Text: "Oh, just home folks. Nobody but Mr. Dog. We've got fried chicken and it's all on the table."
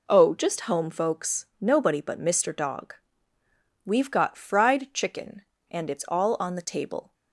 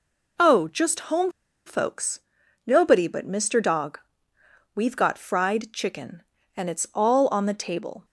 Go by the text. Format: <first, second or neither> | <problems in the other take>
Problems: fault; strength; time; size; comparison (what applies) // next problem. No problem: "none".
first | pauses between "home" and "folks"; slight; at 1.3 s; 0.35 s long